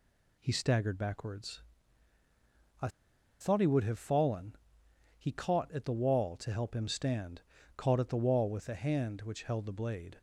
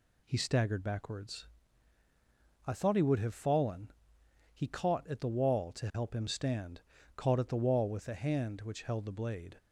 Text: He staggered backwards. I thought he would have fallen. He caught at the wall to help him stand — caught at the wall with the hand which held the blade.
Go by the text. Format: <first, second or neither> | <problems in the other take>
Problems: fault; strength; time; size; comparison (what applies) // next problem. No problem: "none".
second | pauses between "I" and "thought"; noticeable; at 2.8 s; 0.52 s long